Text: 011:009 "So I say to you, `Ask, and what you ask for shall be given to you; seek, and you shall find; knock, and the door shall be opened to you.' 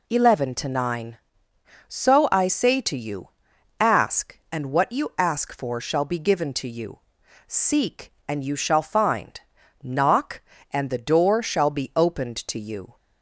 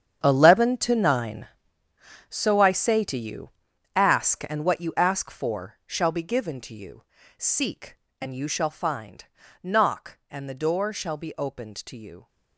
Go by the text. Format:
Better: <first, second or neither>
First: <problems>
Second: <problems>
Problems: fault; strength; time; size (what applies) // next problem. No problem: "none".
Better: first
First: none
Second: gets quieter; strong; throughout; 14.5 dB